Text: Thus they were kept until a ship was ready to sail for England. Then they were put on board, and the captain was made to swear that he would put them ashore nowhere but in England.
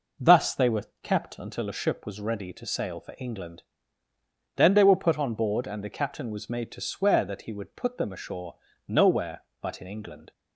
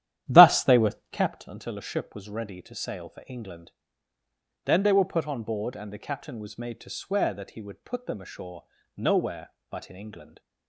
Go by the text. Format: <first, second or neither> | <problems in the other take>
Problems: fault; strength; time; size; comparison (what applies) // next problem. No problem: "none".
first | starts louder than the rest; strong; until 1.3 s; 11.5 dB // pauses between "were" and "kept"; slight; at 0.9 s; 0.18 s long; slight in the first // pauses between "ashore" and "nowhere"; slight; at 8.6 s; 0.32 s long; slight in the first